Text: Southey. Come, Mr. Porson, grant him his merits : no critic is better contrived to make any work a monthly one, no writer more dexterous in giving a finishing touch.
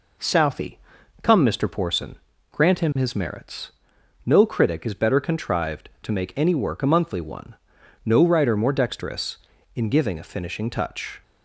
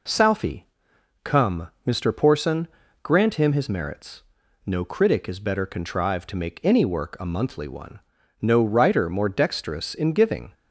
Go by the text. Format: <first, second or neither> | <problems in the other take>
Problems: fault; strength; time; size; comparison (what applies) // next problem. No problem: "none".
first | stops before "a finishing touch"; at 10.5 s